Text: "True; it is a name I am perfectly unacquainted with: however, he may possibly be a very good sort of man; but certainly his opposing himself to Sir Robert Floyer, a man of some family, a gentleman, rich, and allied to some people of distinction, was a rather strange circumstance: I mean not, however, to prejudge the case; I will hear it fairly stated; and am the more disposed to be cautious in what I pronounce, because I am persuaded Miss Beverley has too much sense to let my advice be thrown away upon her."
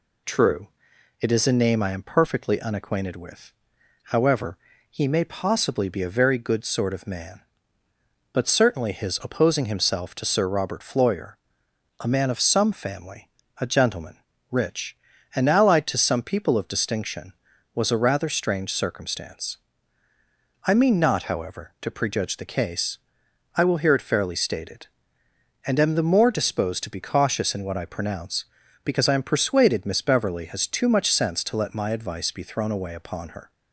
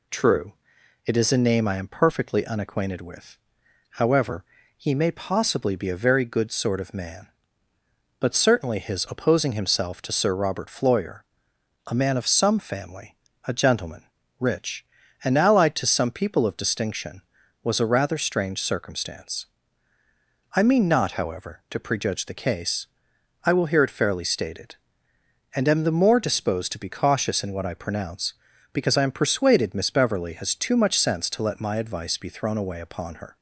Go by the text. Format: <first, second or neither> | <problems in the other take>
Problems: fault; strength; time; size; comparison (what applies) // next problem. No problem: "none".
neither | none